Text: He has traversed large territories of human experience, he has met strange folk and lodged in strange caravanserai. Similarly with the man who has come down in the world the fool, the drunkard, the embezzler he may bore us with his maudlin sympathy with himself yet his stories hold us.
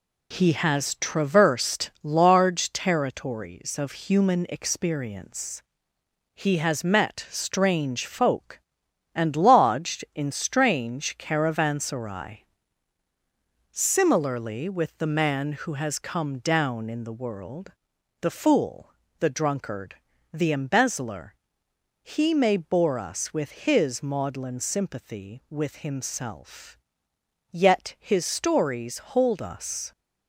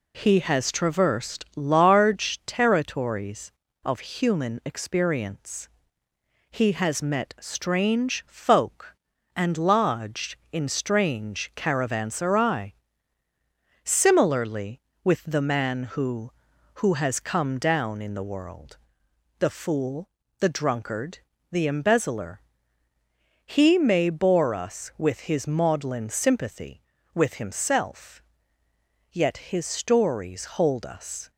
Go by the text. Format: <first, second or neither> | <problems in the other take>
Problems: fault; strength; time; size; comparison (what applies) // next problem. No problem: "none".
first | says "who" twice; at 16.7 s // pauses between "world" and "the"; noticeable; at 18.7 s; 0.62 s long; noticeable in the first // pauses between "embezzler" and "he"; at 22.3 s; 1.0 s long; noticeable in the first // pauses between "himself" and "yet"; noticeable; at 28.2 s; 0.90 s long; noticeable in the first